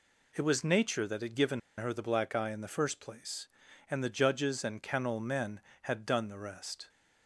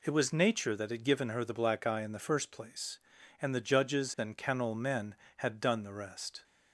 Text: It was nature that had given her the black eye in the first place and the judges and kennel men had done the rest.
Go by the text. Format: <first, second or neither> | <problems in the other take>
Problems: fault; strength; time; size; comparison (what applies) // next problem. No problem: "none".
second | pauses between "given" and "her"; slight; at 1.5 s; 0.18 s long